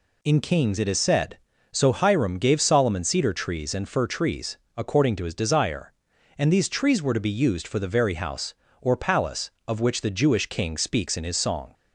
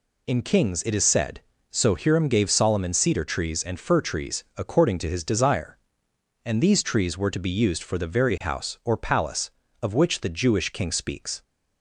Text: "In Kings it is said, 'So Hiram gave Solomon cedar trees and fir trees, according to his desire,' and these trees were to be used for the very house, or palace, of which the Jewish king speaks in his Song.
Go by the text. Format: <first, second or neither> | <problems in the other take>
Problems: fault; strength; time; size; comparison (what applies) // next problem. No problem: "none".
first | stops before "in his Song"; at 11.4 s